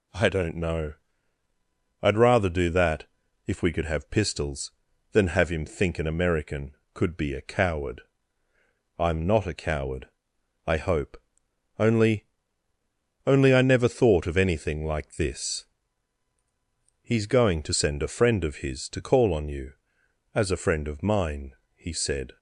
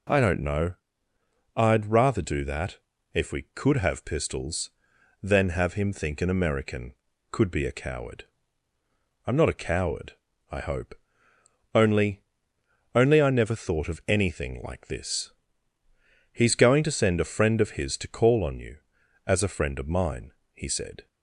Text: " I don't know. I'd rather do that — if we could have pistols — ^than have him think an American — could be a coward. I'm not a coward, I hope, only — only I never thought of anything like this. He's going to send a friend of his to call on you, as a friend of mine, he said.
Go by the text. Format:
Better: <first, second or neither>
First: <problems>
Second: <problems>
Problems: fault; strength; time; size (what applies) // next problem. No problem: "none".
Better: neither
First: none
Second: none